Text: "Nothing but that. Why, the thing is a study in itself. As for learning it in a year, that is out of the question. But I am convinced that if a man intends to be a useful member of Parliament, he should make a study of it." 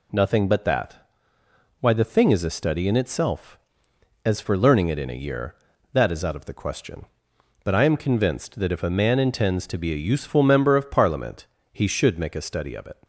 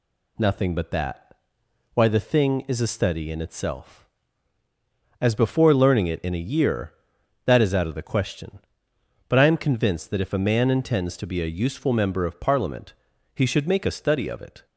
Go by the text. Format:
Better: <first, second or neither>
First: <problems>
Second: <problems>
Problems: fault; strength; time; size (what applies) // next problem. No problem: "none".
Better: first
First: none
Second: says "before" for "for"; at 5.3 s